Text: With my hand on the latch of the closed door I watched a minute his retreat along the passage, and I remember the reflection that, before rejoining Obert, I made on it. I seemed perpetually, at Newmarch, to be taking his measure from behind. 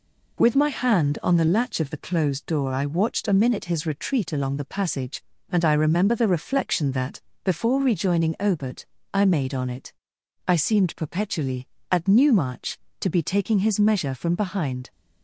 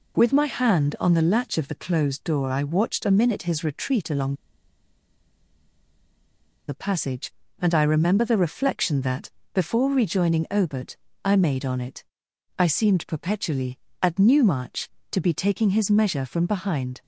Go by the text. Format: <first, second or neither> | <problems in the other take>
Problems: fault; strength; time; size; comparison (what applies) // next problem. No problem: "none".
first | pauses between "along" and "the"; strong; at 4.3 s; 2.3 s long